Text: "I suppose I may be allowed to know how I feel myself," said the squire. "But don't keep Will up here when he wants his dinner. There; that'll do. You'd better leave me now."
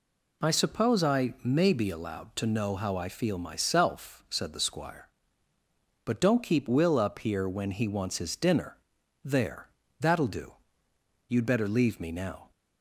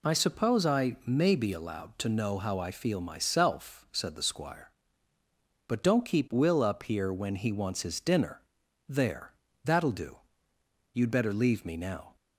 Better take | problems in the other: neither | none

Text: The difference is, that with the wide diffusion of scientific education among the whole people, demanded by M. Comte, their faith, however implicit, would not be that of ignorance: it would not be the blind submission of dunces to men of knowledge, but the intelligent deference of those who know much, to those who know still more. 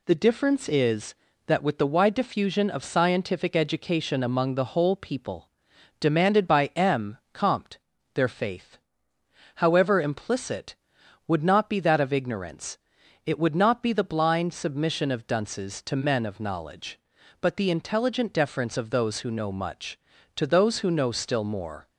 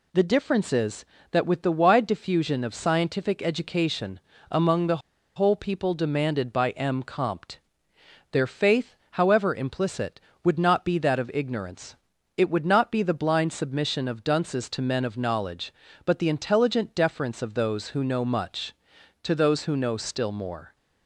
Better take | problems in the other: first | pauses between "education" and "among"; slight; at 4.1 s; 0.32 s long // pauses between "the" and "whole"; at 4.9 s; 0.38 s long

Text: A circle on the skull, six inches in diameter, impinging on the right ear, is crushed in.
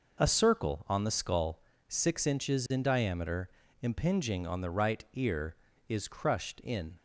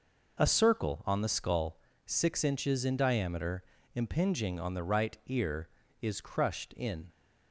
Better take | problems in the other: neither | none

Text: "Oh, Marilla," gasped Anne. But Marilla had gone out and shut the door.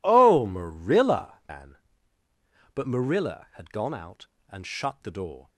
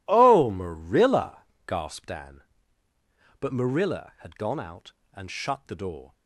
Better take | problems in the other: second | skips "gasped"; at 1.4 s

